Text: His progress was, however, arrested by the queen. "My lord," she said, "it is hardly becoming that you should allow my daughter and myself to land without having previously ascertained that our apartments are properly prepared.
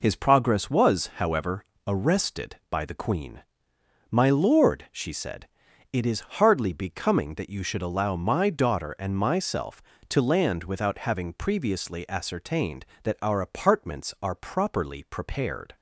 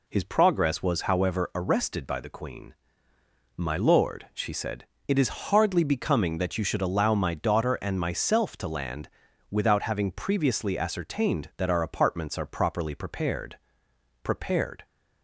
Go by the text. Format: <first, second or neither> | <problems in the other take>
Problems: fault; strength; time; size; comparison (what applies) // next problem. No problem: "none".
first | pauses between "land" and "without"; at 9.0 s; 0.42 s long // says "prepared" twice; at 14.2 s